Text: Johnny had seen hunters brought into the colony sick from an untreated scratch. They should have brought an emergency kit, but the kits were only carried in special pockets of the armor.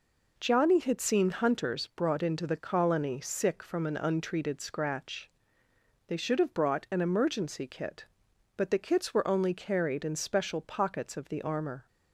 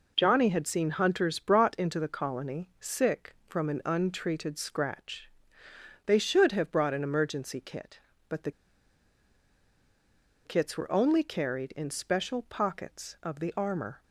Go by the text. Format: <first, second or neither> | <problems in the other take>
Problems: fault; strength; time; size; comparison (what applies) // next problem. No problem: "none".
first | pauses between "the" and "kits"; strong; at 8.5 s; 1.9 s long